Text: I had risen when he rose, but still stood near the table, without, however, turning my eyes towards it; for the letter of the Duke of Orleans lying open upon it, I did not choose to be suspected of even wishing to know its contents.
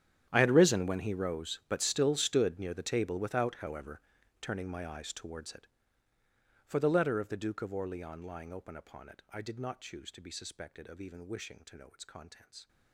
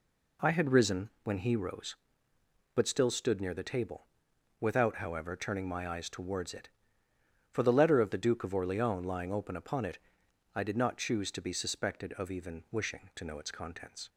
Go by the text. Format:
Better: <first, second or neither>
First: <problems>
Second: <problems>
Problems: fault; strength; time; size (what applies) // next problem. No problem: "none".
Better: second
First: gets quieter; strong; throughout; 20 dB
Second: none